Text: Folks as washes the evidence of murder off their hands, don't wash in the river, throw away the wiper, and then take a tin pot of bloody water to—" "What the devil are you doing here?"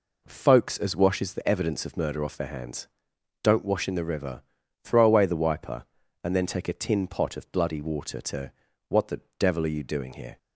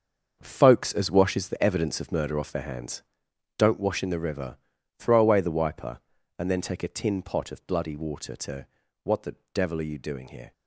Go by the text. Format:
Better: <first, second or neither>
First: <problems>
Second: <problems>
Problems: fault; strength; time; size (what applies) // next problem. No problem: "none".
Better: first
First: pauses between "the" and "devil"; slight; at 9.1 s; 0.18 s long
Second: gets quieter; strong; throughout; 10.5 dB // pauses between "the" and "devil"; slight; at 9.3 s; 0.18 s long